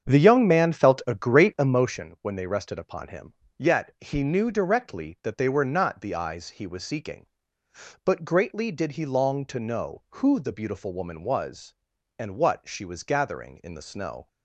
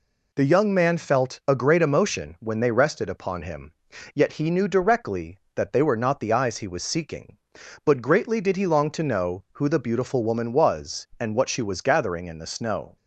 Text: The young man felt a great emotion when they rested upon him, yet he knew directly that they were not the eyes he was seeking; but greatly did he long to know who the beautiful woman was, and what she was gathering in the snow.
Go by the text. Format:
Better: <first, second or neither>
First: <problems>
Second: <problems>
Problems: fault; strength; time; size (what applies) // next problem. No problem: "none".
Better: second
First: starts louder than the rest; strong; until 2.0 s; 7.5 dB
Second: none